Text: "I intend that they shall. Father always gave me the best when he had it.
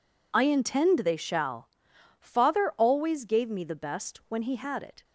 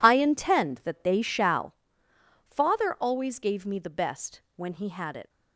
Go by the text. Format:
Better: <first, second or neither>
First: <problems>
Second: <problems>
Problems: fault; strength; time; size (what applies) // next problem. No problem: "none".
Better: second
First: skips "that"; at 0.9 s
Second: none